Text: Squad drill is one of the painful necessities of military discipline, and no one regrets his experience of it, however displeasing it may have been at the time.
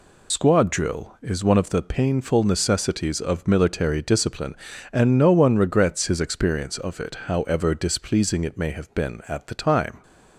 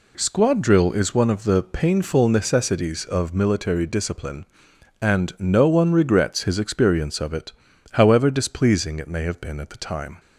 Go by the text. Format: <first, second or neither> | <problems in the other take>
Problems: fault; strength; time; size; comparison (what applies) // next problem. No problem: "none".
second | loses the start of "Squad"; at 0.3 s; 80 ms